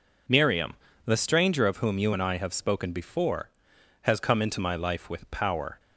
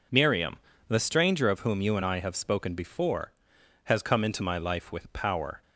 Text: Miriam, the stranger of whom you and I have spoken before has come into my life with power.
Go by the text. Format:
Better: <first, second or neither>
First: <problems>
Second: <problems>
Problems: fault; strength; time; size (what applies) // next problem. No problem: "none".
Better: neither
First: none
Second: none